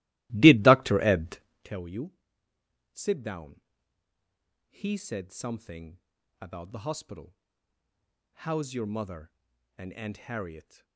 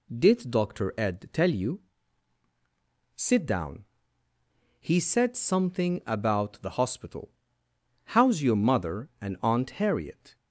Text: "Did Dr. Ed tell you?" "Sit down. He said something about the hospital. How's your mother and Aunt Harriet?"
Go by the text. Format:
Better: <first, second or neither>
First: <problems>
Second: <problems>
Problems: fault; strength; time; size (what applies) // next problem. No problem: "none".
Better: second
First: starts louder than the rest; strong; until 1.7 s; 18 dB // pauses between "Ed" and "tell"; slight; at 1.3 s; 0.26 s long // pauses between "something" and "about"; at 5.9 s; 0.42 s long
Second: none